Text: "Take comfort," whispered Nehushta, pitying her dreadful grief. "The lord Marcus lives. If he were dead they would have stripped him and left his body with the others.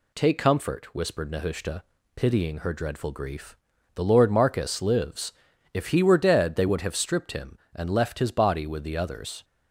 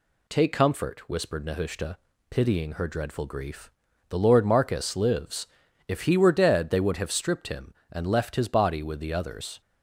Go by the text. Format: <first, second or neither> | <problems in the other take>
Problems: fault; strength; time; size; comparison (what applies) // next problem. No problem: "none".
neither | none